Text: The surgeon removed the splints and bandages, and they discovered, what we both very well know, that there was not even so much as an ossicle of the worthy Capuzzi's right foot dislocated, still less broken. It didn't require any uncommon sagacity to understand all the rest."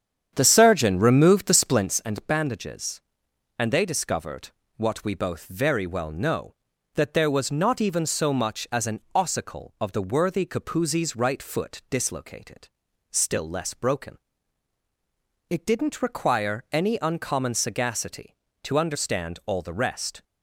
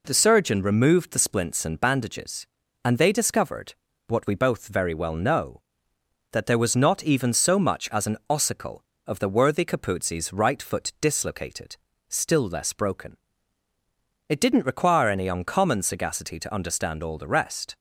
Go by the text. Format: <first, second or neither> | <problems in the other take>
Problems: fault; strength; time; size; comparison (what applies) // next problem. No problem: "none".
second | starts louder than the rest; strong; until 2.0 s; 8.5 dB // pauses between "an" and "ossicle"; slight; at 8.9 s; 0.16 s long